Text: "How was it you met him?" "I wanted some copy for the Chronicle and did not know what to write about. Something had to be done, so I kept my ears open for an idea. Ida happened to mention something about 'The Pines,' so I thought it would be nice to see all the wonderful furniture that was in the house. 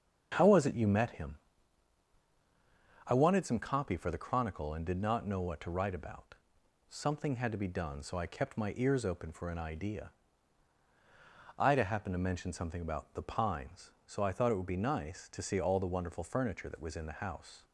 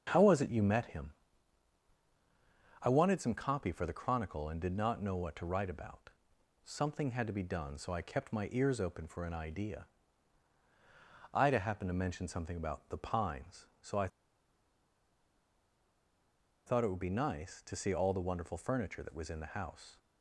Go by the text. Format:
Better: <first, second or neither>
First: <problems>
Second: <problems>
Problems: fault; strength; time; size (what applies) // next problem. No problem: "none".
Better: first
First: starts louder than the rest; until 1.3 s; 6.5 dB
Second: starts louder than the rest; until 1.1 s; 6.5 dB // pauses between "I" and "thought"; strong; at 14.0 s; 2.5 s long